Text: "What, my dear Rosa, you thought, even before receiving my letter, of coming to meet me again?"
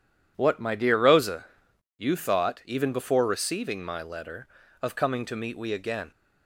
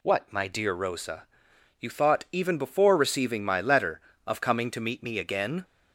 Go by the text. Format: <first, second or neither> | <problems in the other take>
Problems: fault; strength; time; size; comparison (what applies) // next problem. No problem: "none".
second | says "we" for "me"; at 5.5 s